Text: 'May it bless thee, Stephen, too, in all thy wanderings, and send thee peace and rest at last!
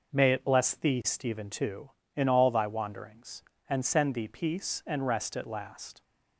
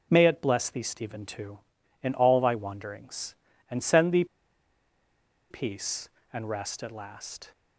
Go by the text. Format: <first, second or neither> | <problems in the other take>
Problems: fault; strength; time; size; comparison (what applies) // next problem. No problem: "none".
first | pauses between "thee" and "peace"; strong; at 4.2 s; 1.2 s long